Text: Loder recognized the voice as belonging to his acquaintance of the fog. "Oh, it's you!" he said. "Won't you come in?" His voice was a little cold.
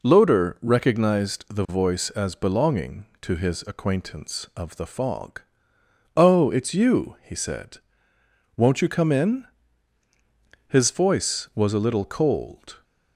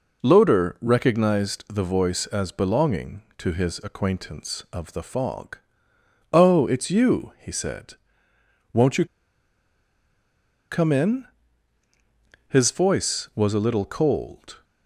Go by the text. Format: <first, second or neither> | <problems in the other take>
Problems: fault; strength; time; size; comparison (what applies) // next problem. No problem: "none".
first | pauses between "you" and "come"; strong; at 9.0 s; 1.6 s long